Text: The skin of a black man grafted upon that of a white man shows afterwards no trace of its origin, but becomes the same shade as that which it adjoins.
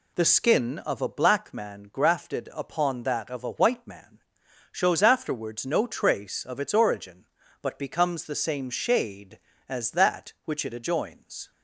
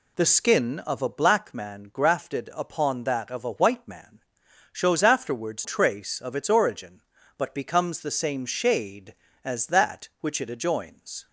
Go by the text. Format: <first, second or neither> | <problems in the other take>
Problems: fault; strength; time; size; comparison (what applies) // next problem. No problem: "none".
first | pauses between "man" and "shows"; noticeable; at 4.2 s; 0.50 s long; noticeable in the first // skips "no"; at 5.6 s